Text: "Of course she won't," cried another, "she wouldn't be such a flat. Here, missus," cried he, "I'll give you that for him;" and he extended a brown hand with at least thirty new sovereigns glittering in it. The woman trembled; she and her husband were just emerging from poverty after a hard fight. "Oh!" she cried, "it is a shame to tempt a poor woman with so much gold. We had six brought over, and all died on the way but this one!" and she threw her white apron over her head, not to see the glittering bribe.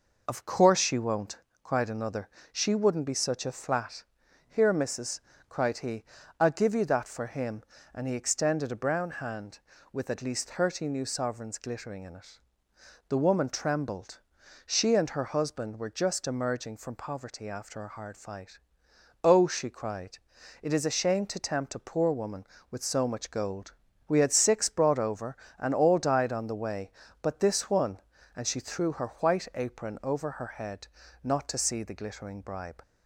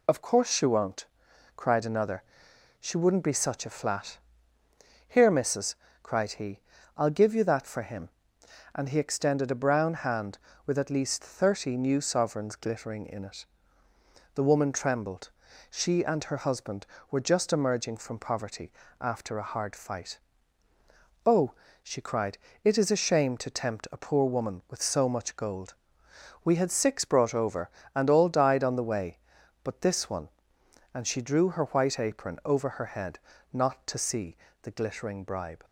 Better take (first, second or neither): first